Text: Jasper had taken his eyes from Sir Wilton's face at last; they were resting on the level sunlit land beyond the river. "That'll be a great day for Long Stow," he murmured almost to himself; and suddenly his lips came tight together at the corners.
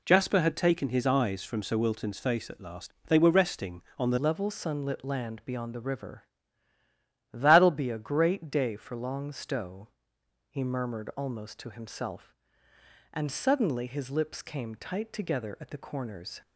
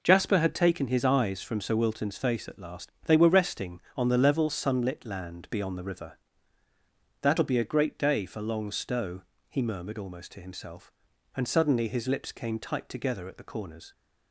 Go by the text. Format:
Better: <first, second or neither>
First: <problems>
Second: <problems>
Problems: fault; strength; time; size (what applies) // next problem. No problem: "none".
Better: second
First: changes voice at "level"; from 4.1 s on; 12.3 s long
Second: none